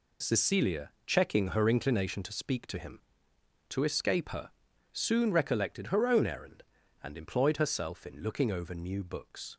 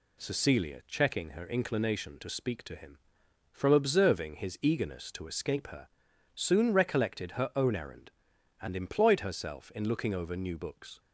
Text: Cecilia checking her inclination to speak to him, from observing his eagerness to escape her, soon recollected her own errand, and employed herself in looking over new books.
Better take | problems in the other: second | pauses between "Cecilia" and "checking"; slight; at 0.8 s; 0.16 s long // skips "from observing his eagerness"; at 3.3 s

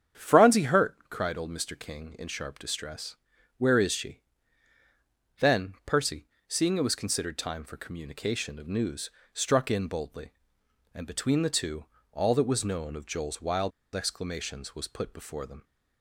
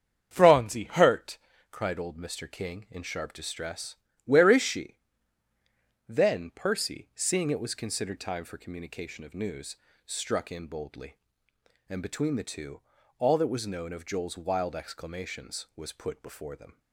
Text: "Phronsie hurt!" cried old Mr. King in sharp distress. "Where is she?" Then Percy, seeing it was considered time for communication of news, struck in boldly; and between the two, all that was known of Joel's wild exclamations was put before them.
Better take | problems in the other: second | starts louder than the rest; strong; until 1.3 s; 8.5 dB; strong in the second // pauses between "wild" and "exclamations"; slight; at 13.7 s; 0.24 s long

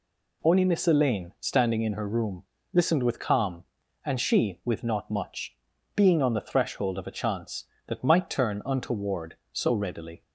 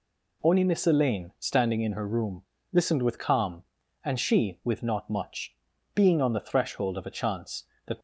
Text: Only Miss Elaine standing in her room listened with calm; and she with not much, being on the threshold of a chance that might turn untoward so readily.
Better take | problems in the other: first | pauses between "room" and "listened"; slight; at 2.4 s; 0.28 s long; slight in the first // stops before "might turn untoward so readily"; at 7.9 s

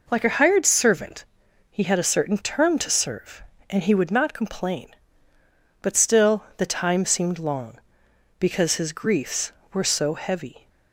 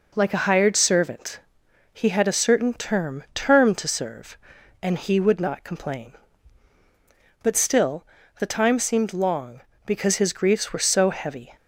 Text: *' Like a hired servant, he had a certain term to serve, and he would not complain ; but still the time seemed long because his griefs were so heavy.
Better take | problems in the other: first | says "term" twice; at 3.3 s // pauses between "still" and "the"; slight; at 8.0 s; 0.32 s long

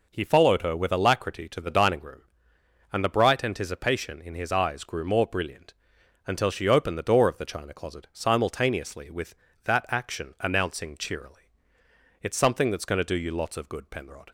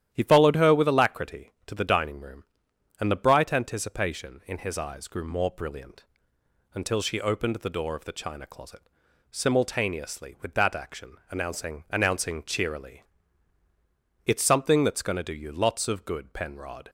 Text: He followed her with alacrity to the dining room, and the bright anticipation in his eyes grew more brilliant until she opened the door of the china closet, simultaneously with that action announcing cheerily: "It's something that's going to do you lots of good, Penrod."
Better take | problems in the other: first | starts louder than the rest; strong; until 1.1 s; 11 dB // pauses between "brilliant" and "until"; noticeable; at 6.0 s; 0.70 s long; noticeable in the first // pauses between "action" and "announcing"; slight; at 11.1 s; 0.16 s long // says "announcing" twice; at 11.8 s

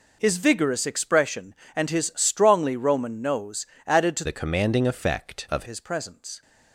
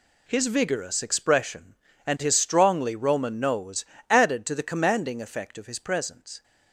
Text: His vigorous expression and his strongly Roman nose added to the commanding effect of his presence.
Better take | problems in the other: second | pauses between "nose" and "added"; slight; at 3.6 s; 0.22 s long; slight in the second // changes voice from "the" to "of"; from 4.2 to 5.6 s; 1.4 s long

